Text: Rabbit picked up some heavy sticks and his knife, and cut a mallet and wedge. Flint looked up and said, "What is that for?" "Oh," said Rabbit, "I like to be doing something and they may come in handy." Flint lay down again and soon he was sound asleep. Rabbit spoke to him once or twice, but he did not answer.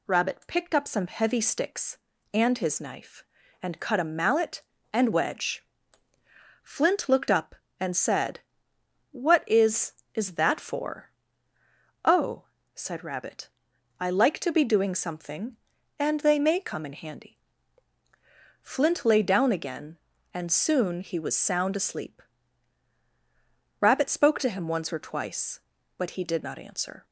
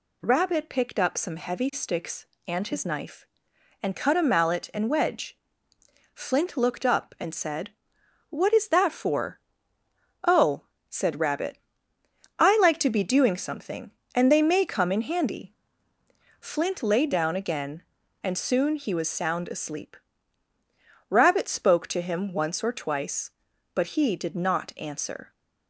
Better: second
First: says "is" twice; at 10.1 s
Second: none

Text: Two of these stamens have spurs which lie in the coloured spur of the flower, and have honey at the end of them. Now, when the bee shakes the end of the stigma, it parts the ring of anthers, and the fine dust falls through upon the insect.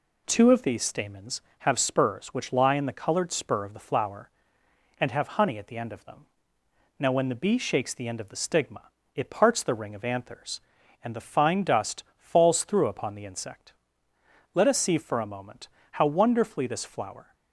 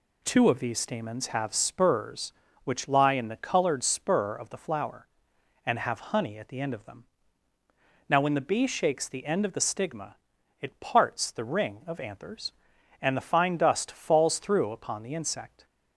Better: second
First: pauses between "dust" and "falls"; slight; at 12.0 s; 0.16 s long // goes on to say "Let us see for a moment how wonderfully this flower"; strong; from 14.5 s on; 2.8 s long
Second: none

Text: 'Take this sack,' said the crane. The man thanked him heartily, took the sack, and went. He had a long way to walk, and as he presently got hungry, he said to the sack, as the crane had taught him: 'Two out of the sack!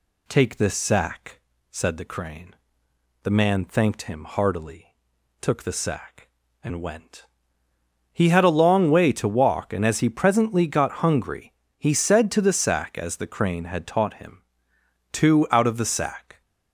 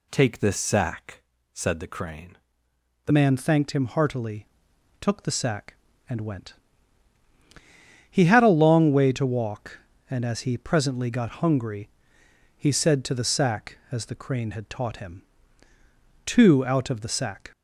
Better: first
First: none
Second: changes voice at "man"; from 3.1 s on; 14.4 s long

